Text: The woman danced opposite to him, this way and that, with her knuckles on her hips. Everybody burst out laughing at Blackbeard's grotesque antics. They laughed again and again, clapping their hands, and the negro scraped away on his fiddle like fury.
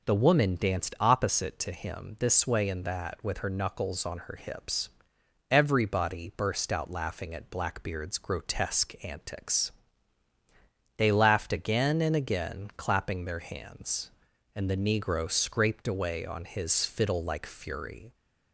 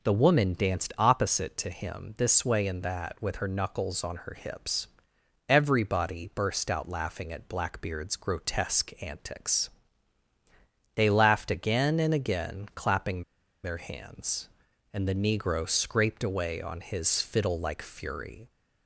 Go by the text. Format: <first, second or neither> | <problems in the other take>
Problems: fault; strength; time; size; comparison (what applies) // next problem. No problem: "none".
first | pauses between "clapping" and "their"; at 13.2 s; 0.41 s long